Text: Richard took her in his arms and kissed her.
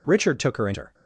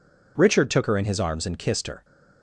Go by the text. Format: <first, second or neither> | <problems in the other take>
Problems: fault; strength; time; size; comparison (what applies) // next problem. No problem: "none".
second | skips "his arms and kissed"; at 0.7 s